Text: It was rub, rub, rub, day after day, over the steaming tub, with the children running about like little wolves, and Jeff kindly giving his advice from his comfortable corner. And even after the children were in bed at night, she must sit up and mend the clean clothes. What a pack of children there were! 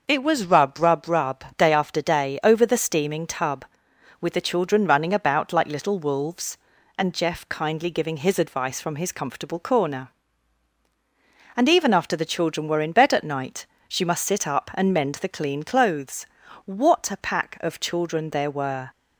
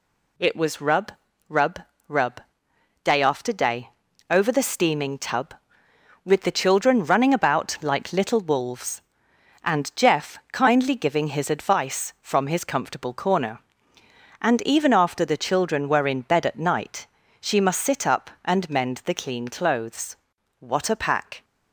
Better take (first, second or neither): first